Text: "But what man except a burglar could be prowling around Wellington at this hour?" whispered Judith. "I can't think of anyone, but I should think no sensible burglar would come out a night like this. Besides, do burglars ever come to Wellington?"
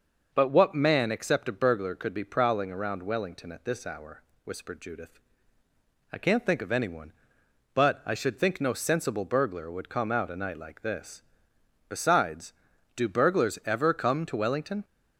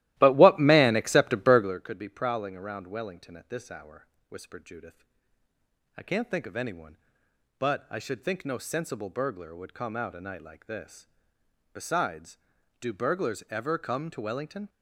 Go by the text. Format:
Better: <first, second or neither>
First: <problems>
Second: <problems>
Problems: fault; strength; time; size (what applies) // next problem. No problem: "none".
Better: first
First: none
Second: starts louder than the rest; strong; until 1.8 s; 15.5 dB